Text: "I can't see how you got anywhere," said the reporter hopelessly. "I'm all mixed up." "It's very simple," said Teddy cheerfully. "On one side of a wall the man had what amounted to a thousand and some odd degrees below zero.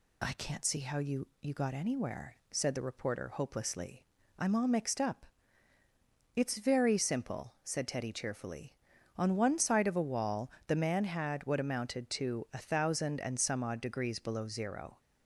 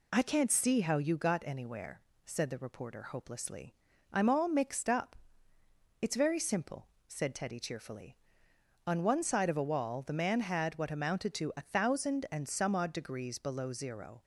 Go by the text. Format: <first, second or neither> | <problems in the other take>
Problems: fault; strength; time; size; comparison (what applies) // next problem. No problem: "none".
second | says "you" twice; at 1.4 s // pauses between "wall" and "the"; slight; at 10.4 s; 0.20 s long